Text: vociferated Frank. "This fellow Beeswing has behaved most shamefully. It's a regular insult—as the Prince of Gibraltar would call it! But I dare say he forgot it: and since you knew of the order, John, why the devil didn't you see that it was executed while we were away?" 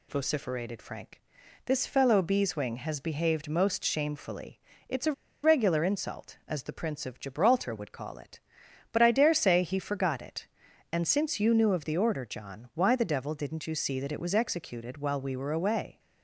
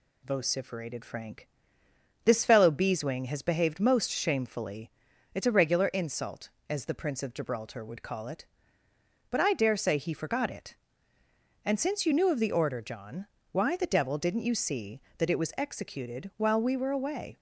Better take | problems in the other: second | pauses between "a" and "regular"; slight; at 5.1 s; 0.31 s long

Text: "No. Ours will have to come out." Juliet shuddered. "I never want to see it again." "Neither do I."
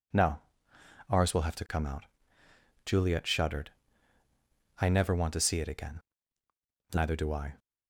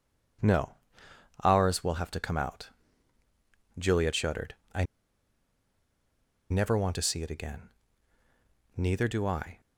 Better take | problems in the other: first | pauses between "I" and "never"; strong; at 4.8 s; 1.6 s long

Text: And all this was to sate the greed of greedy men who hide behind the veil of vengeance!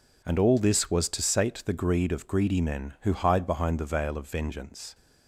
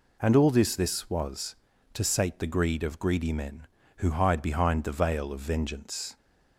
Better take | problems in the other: first | says "this" twice; at 0.7 s

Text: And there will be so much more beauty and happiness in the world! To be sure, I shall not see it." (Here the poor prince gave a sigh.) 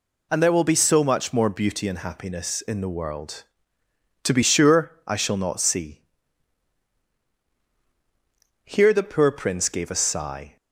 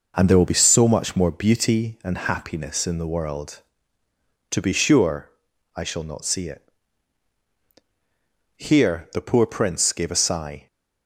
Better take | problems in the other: second | skips "it"; at 7.3 s

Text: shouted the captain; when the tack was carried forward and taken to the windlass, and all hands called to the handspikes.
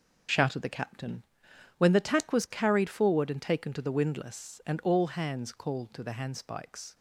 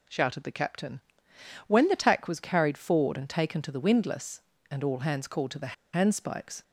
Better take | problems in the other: first | pauses between "the" and "handspikes"; slight; at 5.7 s; 0.19 s long

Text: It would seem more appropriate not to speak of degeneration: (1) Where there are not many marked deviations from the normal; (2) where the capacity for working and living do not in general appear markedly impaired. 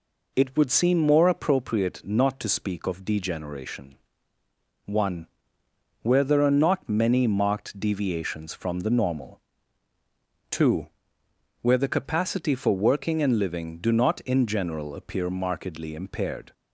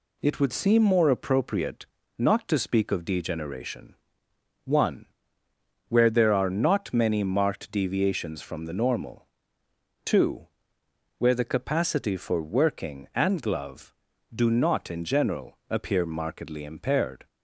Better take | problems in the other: first | pauses between "appropriate" and "not"; slight; at 1.8 s; 0.30 s long // says "glove" for "living"; at 13.4 s

